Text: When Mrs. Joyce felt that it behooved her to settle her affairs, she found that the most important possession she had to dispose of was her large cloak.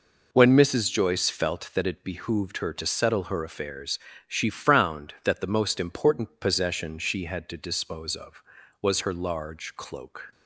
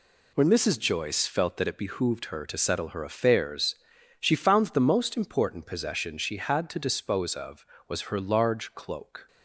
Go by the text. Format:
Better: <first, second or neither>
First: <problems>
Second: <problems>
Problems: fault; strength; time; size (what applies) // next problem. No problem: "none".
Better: second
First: says "frowned" for "found"; at 4.4 s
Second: none